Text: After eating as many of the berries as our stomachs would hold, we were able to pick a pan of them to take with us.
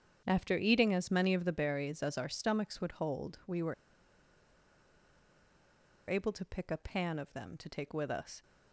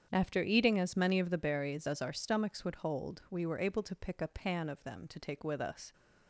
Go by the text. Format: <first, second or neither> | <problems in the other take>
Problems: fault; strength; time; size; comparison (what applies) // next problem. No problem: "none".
second | starts louder than the rest; strong; until 1.2 s; 8 dB; strong in the second // pauses between "were" and "able"; strong; at 3.7 s; 2.3 s long